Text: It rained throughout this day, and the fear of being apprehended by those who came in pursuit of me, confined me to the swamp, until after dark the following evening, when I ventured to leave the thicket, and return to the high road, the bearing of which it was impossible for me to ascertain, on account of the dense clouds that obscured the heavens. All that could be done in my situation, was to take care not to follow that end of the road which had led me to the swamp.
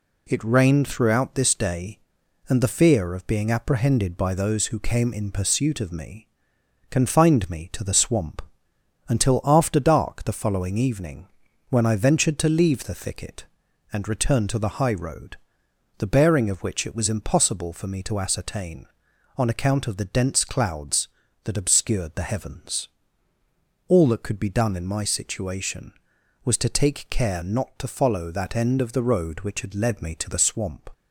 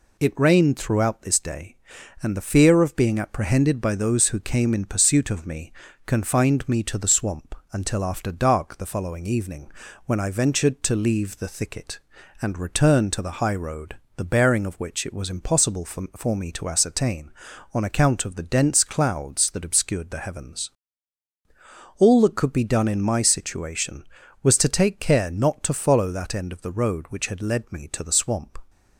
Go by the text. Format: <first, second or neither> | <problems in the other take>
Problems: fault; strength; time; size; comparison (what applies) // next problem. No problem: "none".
first | says "for" twice; at 16.1 s